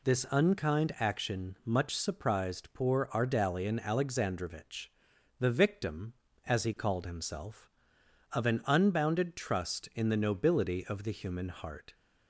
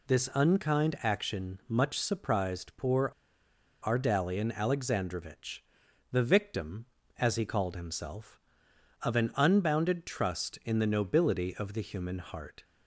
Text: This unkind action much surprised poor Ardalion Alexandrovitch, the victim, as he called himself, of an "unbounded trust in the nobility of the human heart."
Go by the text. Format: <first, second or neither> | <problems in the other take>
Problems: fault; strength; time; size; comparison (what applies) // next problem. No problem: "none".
first | pauses between "poor" and "Ardalion"; noticeable; at 3.1 s; 0.72 s long